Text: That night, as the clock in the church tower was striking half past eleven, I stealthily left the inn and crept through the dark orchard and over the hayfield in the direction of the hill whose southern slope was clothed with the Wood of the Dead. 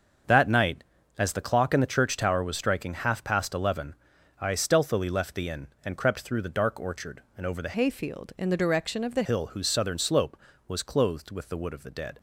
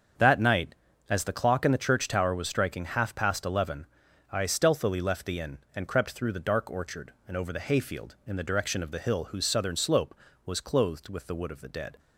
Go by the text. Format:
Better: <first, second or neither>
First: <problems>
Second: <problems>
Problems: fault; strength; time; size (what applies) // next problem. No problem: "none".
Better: second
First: starts louder than the rest; until 1.6 s; 6.5 dB // changes voice from "hayfield" to "the"; from 7.7 to 9.2 s; 1.5 s long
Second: starts louder than the rest; until 1.5 s; 7 dB